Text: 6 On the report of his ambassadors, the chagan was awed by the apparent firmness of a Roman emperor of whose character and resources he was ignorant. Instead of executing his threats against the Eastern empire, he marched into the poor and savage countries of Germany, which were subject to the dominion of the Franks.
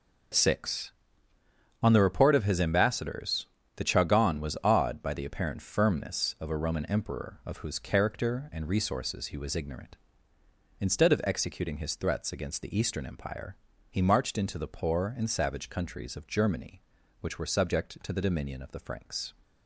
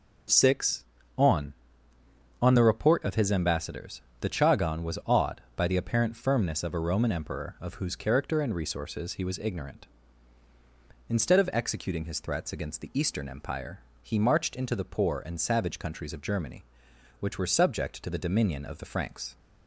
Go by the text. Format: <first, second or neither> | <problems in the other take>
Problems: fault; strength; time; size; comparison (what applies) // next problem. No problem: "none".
first | says "On" twice; at 2.3 s